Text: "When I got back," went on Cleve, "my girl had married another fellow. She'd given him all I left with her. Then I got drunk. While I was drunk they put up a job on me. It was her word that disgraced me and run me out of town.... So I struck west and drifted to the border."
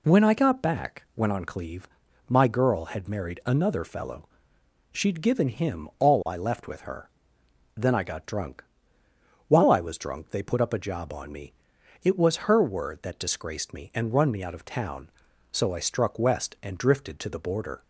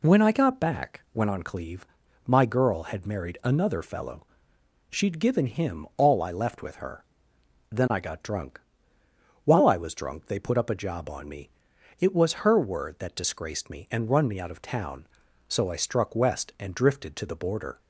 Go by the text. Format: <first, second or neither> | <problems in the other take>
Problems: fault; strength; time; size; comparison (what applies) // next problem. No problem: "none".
neither | none